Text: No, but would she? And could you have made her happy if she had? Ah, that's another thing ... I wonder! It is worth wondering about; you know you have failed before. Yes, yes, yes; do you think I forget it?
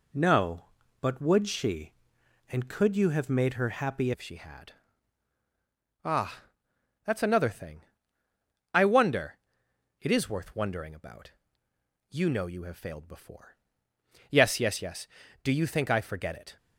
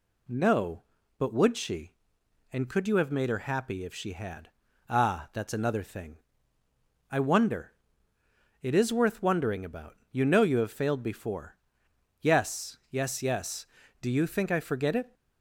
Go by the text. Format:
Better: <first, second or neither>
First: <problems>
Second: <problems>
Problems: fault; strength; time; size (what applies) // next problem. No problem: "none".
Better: second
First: changes voice at "if"; from 4.1 s on; 12.4 s long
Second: none